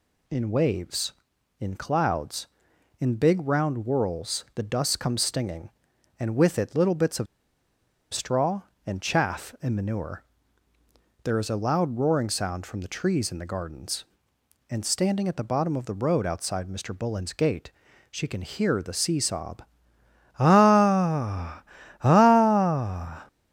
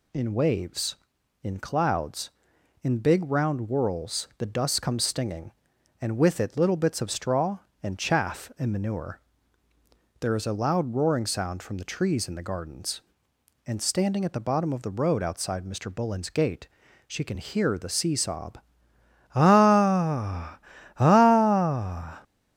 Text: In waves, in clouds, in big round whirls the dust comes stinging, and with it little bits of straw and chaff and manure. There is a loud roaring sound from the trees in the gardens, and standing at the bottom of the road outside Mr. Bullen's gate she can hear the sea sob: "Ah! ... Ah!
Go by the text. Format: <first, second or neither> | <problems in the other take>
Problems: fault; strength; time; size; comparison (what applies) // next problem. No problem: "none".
second | pauses between "of" and "straw"; noticeable; at 7.2 s; 0.87 s long // pauses between "gate" and "she"; at 17.7 s; 0.38 s long; also in the second